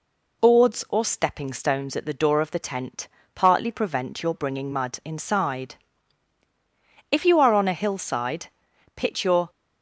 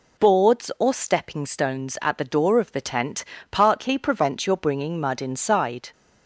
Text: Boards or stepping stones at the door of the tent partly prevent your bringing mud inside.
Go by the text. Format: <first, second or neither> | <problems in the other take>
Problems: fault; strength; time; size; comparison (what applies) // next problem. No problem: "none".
second | pauses between "tent" and "partly"; slight; at 3.0 s; 0.26 s long; slight in the second // goes on to say "If you are on a hillside pitch your"; strong; from 7.0 s on; 2.4 s long